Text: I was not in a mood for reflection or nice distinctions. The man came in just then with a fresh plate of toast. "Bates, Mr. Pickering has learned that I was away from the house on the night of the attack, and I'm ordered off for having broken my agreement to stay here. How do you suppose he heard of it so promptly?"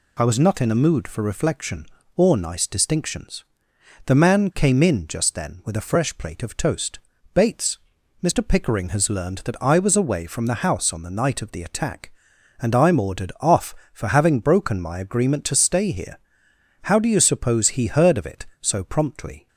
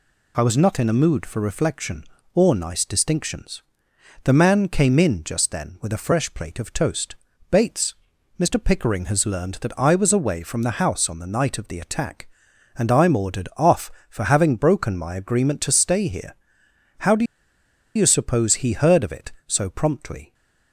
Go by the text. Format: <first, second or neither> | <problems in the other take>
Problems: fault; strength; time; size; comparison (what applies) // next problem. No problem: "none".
first | pauses between "do" and "you"; noticeable; at 17.2 s; 0.71 s long